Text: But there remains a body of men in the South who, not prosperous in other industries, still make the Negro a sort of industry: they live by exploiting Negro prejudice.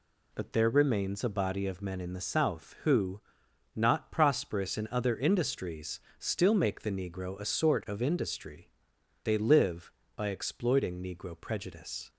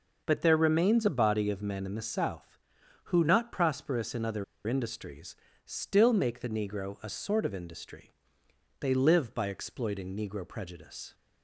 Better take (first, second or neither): first